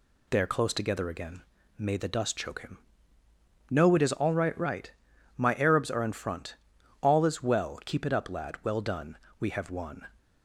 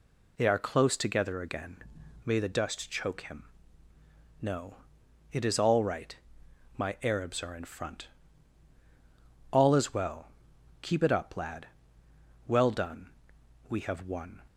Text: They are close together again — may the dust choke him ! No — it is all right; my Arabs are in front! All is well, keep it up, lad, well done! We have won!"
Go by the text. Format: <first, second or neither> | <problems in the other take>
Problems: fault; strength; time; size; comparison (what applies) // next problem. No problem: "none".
second | says "right" twice; at 4.5 s